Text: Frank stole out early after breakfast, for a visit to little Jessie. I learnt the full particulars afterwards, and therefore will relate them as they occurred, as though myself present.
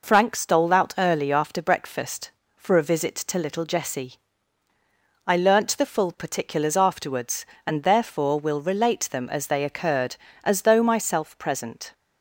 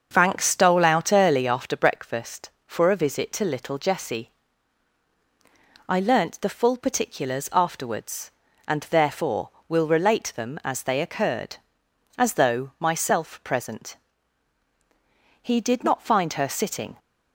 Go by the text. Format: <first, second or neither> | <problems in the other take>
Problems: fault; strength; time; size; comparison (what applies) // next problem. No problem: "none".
first | starts louder than the rest; until 1.1 s; 6 dB // goes on to say "He did not find her sitting"; from 15.4 s on; 1.5 s long